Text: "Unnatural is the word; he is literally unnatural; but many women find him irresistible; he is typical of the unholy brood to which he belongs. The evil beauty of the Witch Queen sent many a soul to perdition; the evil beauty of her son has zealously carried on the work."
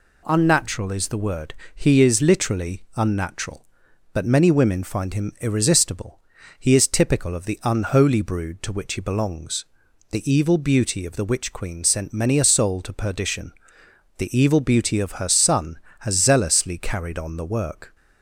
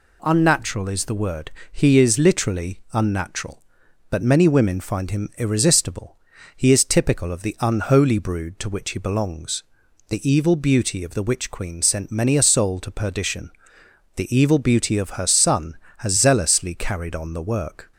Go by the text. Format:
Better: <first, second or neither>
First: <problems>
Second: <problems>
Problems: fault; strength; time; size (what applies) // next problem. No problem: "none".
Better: neither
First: none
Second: none